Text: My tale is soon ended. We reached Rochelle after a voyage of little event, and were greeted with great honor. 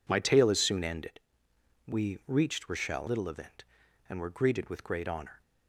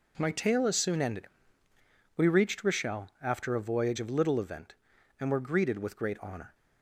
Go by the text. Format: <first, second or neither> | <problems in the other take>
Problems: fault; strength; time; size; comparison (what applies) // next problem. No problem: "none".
second | skips "after a voyage of"; at 3.0 s